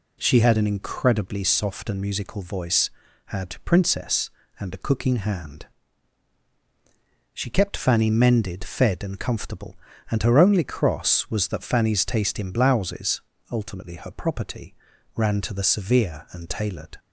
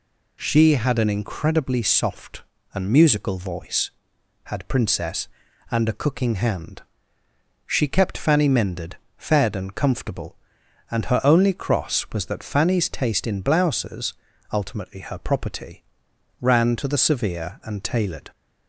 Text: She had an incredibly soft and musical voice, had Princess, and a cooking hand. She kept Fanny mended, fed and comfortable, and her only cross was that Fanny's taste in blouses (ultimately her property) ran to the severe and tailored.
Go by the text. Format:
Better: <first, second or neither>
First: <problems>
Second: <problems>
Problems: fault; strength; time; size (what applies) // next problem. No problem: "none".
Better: neither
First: none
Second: none